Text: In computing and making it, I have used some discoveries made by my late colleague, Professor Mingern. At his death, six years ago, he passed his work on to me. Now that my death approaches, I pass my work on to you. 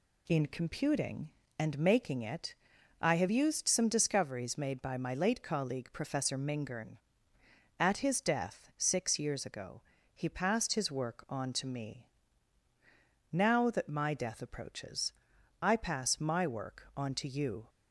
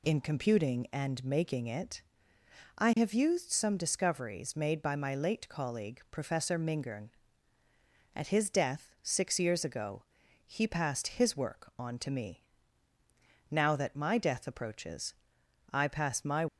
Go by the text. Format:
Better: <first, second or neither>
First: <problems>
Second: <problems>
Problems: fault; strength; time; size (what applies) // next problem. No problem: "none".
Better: first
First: none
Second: stops before "work on to you"; at 16.4 s